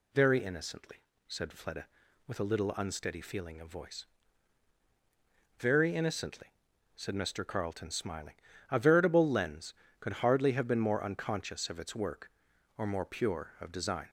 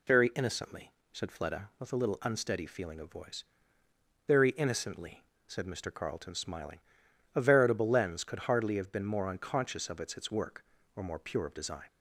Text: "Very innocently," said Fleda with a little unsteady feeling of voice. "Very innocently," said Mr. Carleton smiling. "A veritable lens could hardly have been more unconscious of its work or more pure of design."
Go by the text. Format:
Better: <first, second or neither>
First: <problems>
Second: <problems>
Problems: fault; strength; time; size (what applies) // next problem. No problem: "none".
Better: first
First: none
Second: says "its" twice; at 10.1 s